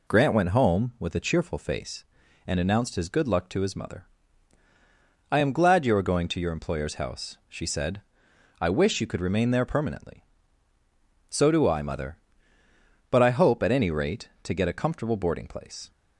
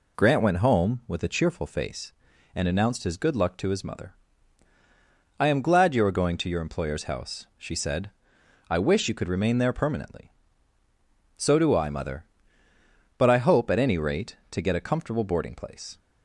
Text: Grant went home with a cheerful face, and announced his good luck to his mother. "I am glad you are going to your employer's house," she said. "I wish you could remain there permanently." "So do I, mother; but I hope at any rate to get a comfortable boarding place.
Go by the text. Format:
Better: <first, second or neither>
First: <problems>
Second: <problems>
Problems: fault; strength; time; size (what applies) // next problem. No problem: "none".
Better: neither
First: none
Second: none